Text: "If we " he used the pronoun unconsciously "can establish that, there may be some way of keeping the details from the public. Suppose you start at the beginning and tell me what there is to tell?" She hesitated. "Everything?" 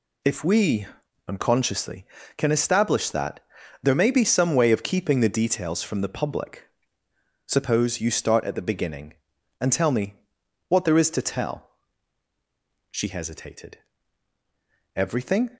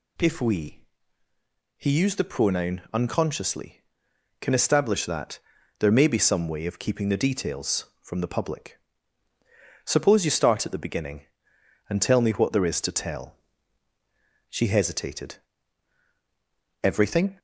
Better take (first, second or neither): second